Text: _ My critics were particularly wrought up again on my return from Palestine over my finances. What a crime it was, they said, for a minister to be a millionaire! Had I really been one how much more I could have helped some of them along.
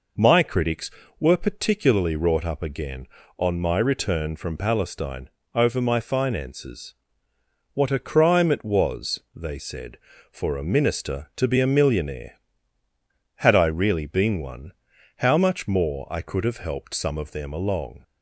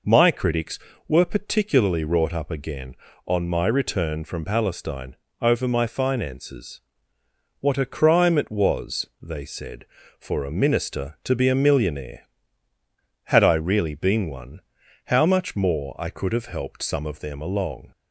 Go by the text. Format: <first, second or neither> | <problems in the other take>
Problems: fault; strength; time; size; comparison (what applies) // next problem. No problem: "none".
neither | pauses between "Palestine" and "over"; slight; the same in both // pauses between "one" and "how"; noticeable; the same in both